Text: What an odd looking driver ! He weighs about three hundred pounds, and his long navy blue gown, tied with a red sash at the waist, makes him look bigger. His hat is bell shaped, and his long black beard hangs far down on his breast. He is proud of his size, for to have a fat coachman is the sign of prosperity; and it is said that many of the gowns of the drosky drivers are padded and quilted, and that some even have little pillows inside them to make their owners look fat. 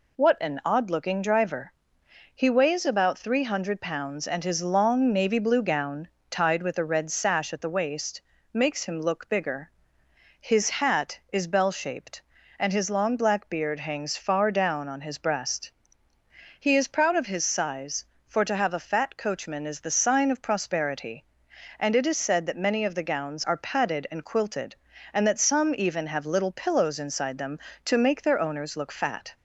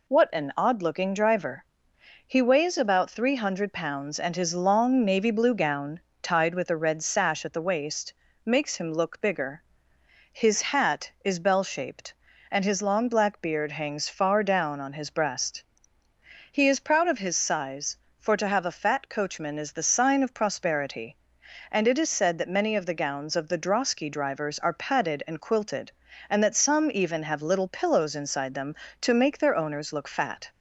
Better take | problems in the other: second | skips "of the drosky drivers"; at 23.4 s

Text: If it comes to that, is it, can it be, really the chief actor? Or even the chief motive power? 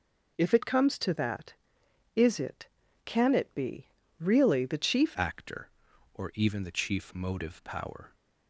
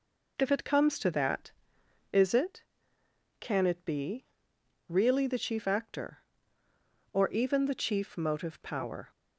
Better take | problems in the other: second | changes voice at "actor"; from 5.1 s on; 3.0 s long

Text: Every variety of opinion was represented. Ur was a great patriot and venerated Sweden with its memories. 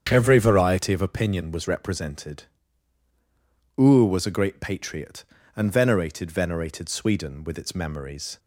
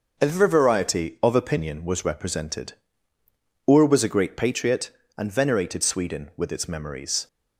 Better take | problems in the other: second | starts louder than the rest; strong; until 1.1 s; 8 dB // says "venerated" twice; at 6.3 s

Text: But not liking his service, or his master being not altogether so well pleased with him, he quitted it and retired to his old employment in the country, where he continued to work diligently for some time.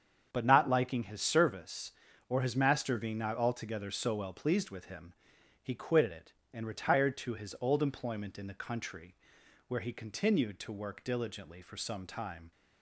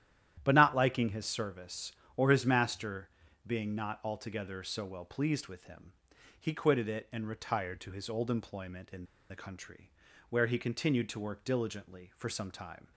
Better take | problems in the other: first | starts louder than the rest; strong; until 1.4 s; 11.5 dB; strong in the first // pauses between "master" and "being"; at 3.0 s; 0.38 s long // pauses between "in" and "the"; slight; at 9.0 s; 0.25 s long

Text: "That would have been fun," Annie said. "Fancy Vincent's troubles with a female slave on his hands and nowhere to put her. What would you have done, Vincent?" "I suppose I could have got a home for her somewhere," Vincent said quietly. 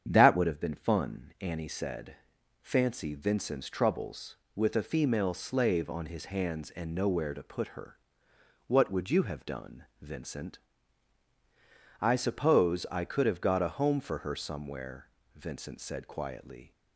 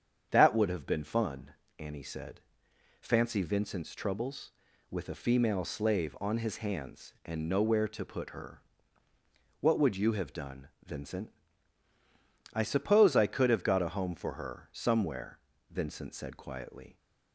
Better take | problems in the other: neither | starts louder than the rest; strong; the same in both

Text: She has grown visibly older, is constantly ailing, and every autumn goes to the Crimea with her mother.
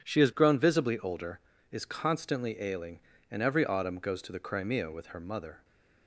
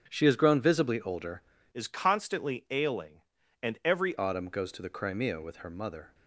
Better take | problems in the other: first | starts louder than the rest; strong; until 1.1 s; 7.5 dB // changes voice from "is" to "every"; from 1.7 to 4.1 s; 2.4 s long

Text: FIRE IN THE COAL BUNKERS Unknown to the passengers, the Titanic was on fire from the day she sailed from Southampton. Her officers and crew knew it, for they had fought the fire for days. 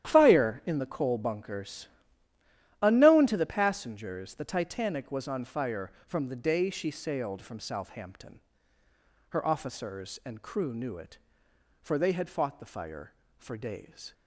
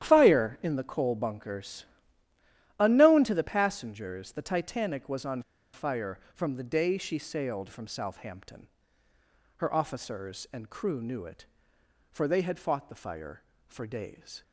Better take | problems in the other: first | starts louder than the rest; strong; until 1.0 s; 10.5 dB; strong in the first // pauses between "BUNKERS" and "Unknown"; noticeable; at 1.8 s; 0.96 s long; noticeable in the first // pauses between "on" and "fire"; slight; at 5.4 s; 0.31 s long

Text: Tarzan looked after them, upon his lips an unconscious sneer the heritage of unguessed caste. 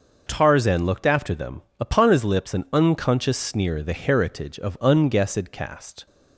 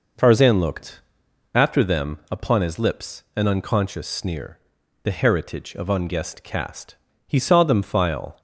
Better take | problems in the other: first | pauses between "looked" and "after"; noticeable; at 1.0 s; 0.52 s long // pauses between "sneer" and "the"; at 4.5 s; 0.44 s long // goes on to say "He saw them file"; noticeable; from 7.2 s on; 1.1 s long

